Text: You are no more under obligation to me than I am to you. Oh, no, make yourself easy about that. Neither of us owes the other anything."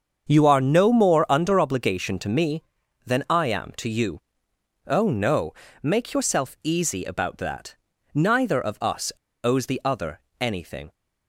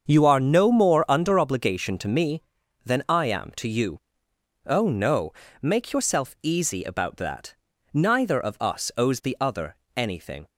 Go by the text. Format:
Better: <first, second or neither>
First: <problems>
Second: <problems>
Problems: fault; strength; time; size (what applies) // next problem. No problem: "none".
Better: second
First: starts louder than the rest; strong; until 1.3 s; 7 dB // pauses between "us" and "owes"; slight; at 9.0 s; 0.33 s long // pauses between "other" and "anything"; slight; at 10.1 s; 0.20 s long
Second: starts louder than the rest; strong; until 1.1 s; 7 dB // pauses between "other" and "anything"; slight; at 9.7 s; 0.20 s long